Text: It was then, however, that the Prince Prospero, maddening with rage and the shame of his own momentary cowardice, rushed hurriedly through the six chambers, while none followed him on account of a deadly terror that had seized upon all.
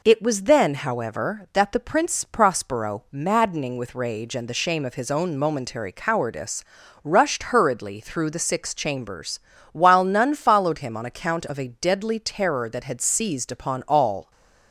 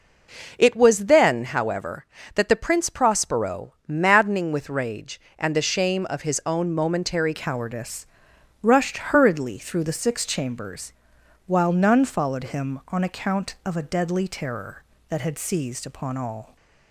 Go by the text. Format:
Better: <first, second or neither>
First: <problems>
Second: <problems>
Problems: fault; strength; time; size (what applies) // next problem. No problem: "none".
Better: first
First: none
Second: changes voice at "cowardice"; from 7.3 s on; 9.2 s long